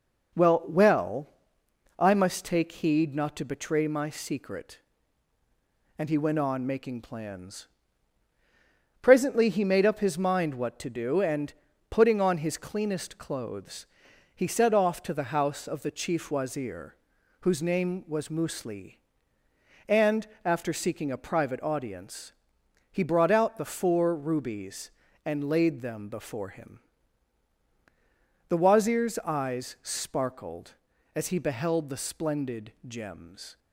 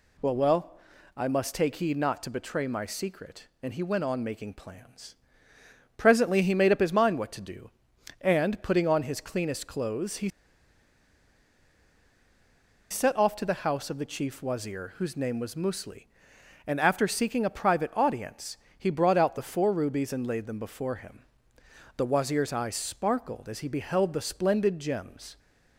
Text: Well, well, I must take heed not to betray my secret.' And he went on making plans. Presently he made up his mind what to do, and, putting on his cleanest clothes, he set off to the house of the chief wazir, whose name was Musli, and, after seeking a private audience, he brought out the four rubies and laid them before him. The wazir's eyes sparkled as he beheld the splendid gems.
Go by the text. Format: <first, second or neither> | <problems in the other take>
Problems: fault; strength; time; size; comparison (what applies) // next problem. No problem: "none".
first | pauses between "he" and "set"; strong; at 10.2 s; 2.6 s long